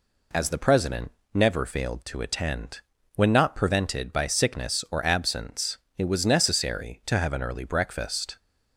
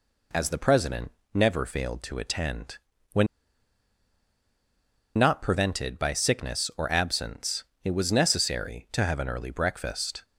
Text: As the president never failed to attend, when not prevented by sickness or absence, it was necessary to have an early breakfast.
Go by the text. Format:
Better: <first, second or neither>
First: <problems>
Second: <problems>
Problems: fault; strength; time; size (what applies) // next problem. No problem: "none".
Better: first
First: pauses between "president" and "never"; slight; at 1.1 s; 0.22 s long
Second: pauses between "president" and "never"; slight; at 1.1 s; 0.22 s long // pauses between "when" and "not"; strong; at 3.2 s; 1.9 s long